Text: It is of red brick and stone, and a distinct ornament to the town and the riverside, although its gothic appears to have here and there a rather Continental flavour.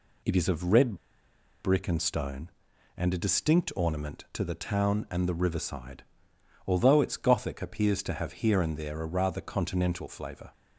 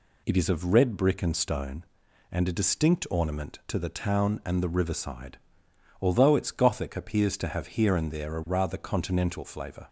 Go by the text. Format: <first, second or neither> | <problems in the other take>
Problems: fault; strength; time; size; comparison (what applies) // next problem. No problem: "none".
second | pauses between "red" and "brick"; noticeable; at 0.9 s; 0.69 s long